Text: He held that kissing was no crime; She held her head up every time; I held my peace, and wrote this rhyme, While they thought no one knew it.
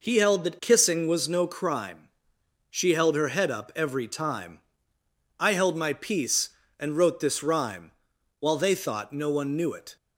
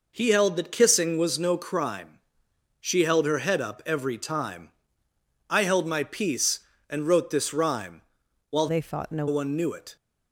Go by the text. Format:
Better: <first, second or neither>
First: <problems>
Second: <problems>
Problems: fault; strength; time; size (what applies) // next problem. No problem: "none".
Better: first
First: none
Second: changes voice from "they" to "no"; from 8.6 to 9.2 s; 0.6 s long